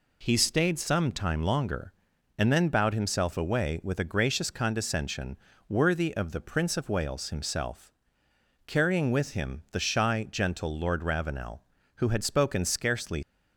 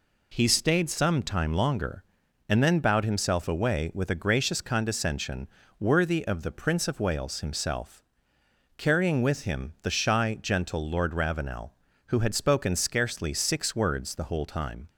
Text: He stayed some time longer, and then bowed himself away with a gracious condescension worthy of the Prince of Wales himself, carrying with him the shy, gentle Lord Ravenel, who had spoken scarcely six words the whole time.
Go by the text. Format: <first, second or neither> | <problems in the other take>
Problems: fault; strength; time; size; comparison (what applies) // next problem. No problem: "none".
second | pauses between "condescension" and "worthy"; slight; at 5.3 s; 0.32 s long; slight in the second // stops before "six words the whole time"; at 13.2 s